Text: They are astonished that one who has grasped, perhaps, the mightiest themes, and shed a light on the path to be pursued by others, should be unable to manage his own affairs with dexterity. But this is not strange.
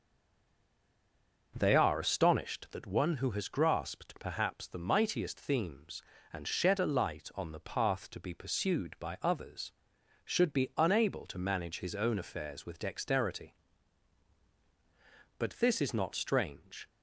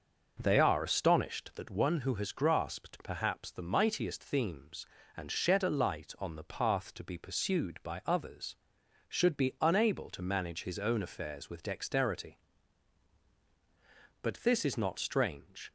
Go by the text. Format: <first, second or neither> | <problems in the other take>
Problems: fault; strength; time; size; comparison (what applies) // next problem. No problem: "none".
second | stays silent before the first word; noticeable; until 1.5 s; 1.5 s long